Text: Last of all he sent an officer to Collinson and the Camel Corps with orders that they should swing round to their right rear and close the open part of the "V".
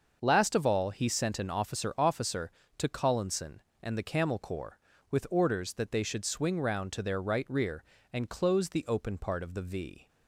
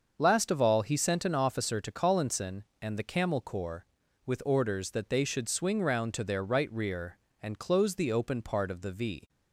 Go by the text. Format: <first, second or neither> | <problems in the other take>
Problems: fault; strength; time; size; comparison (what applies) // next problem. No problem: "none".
second | starts louder than the rest; until 1.2 s; 6.5 dB; also in the second // says "officer" twice; at 1.9 s